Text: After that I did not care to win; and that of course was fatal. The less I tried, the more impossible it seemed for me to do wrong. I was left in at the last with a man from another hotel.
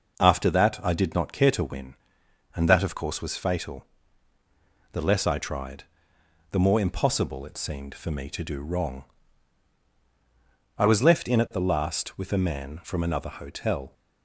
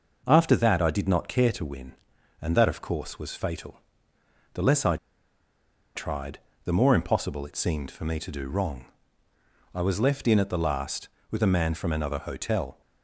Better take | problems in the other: first | pauses between "I" and "tried"; at 4.9 s; 0.99 s long

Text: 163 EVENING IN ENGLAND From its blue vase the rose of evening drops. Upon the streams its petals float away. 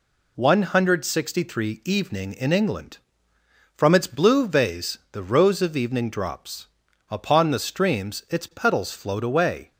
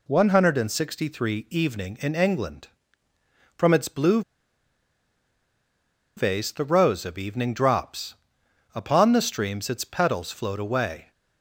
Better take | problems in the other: first | pauses between "blue" and "vase"; strong; at 4.2 s; 1.9 s long

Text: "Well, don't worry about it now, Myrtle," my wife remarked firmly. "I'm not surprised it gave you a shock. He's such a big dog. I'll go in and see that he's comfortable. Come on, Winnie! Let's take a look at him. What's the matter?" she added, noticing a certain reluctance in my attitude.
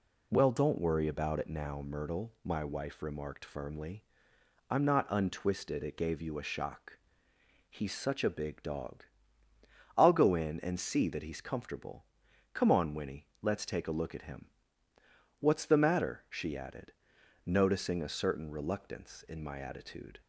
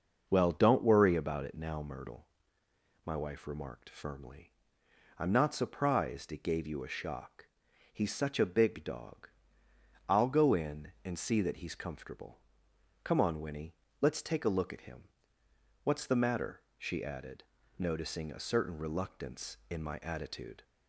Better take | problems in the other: second | says "untwisted" for "surprised"; at 5.1 s

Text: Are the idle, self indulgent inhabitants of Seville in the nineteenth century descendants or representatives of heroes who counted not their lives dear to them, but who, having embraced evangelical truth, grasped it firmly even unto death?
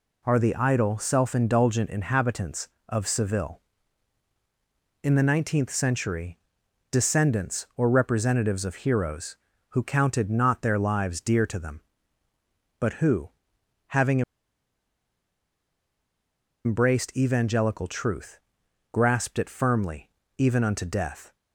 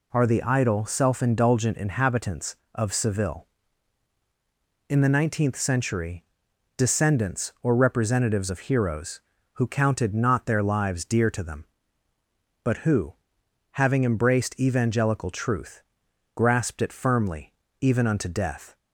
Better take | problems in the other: second | pauses between "century" and "descendants"; noticeable; at 6.3 s; 0.52 s long; noticeable in the second // pauses between "having" and "embraced"; strong; at 14.2 s; 2.4 s long // pauses between "firmly" and "even"; slight; at 20.0 s; 0.30 s long; slight in the second

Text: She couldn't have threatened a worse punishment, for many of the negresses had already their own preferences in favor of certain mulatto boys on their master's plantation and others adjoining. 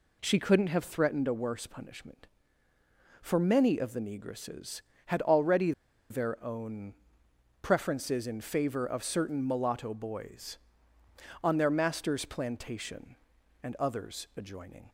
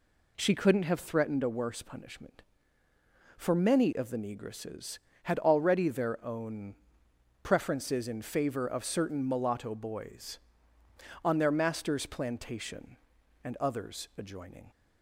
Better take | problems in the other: second | pauses between "already" and "their"; at 5.7 s; 0.38 s long // pauses between "own" and "preferences"; noticeable; at 6.9 s; 0.68 s long; noticeable in the second

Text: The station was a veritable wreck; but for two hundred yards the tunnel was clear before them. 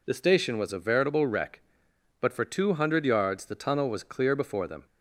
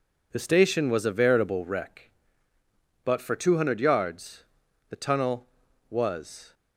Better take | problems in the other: first | pauses between "yards" and "the"; at 4.4 s; 0.44 s long // stops before "clear before them"; at 6.5 s

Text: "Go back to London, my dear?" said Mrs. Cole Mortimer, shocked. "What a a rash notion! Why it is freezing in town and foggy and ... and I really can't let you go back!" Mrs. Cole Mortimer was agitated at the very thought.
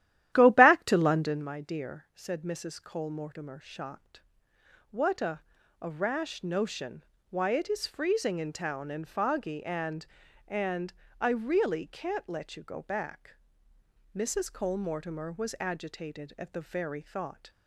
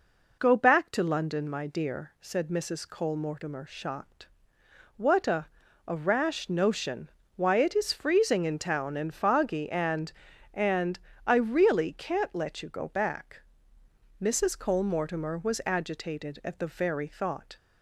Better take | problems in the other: second | starts louder than the rest; strong; until 1.5 s; 12.5 dB // pauses between "a" and "a"; at 5.4 s; 0.40 s long; also in the second // pauses between "and" and "I"; slight; at 10.9 s; 0.30 s long; slight in the second

